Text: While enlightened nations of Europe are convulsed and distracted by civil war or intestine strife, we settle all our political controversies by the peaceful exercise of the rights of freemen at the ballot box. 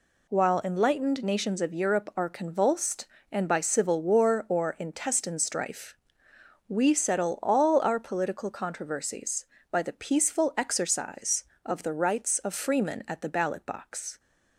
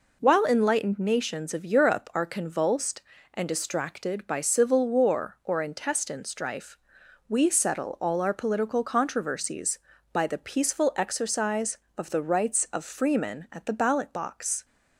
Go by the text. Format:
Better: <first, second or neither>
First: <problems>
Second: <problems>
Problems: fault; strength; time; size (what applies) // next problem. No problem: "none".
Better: second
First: skips "distracted"; at 3.4 s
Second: none